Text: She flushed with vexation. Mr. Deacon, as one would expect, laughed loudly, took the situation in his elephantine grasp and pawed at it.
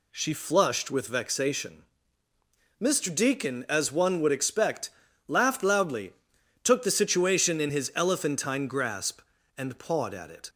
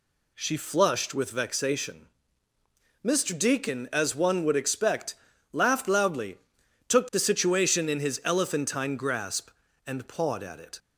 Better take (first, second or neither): neither